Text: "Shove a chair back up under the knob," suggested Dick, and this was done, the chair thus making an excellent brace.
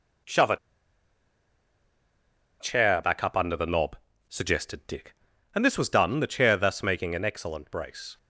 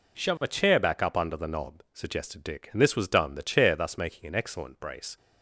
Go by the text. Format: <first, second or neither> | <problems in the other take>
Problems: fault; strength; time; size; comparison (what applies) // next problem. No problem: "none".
second | pauses between "a" and "chair"; strong; at 0.5 s; 2.0 s long